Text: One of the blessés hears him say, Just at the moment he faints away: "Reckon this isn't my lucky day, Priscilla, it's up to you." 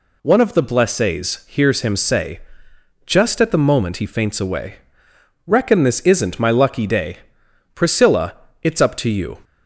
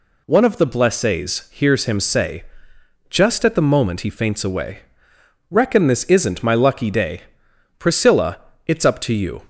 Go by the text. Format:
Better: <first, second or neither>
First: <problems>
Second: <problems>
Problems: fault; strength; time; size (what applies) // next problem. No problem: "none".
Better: neither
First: none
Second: none